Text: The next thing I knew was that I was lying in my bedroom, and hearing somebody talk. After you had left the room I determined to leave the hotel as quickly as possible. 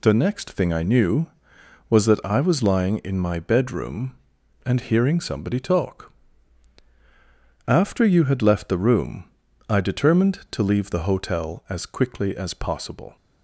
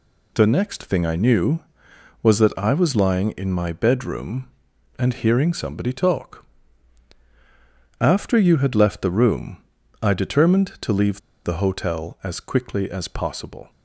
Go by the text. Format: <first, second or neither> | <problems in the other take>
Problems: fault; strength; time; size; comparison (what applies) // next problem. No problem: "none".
first | pauses between "room" and "I"; at 9.5 s; 0.44 s long; also in the first // pauses between "leave" and "the"; slight; at 11.1 s; 0.25 s long